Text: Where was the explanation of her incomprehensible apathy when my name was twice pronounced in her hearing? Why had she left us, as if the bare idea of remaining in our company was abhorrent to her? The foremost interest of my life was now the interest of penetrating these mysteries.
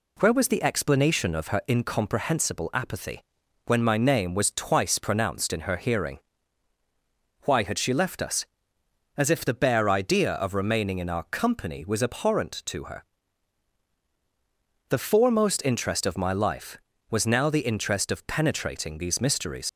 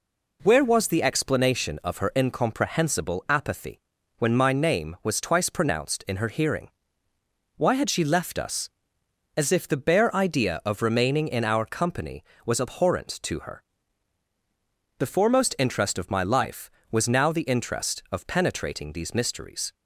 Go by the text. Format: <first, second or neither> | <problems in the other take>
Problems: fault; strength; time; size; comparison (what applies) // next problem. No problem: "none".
second | pauses between "apathy" and "when"; at 3.2 s; 0.44 s long; also in the second // leaves "mysteries" unfinished; at 19.6 s; 60 ms